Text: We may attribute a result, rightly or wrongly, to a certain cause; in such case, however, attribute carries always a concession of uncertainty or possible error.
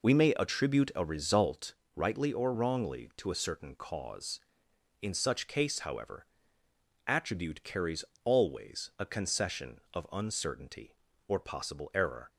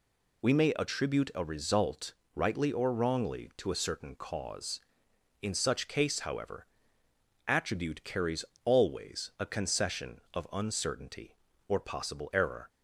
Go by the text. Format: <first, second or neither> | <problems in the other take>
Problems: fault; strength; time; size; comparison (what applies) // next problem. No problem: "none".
second | starts louder than the rest; noticeable; until 1.6 s; 4.5 dB // pauses between "carries" and "always"; slight; at 8.0 s; 0.20 s long; slight in the second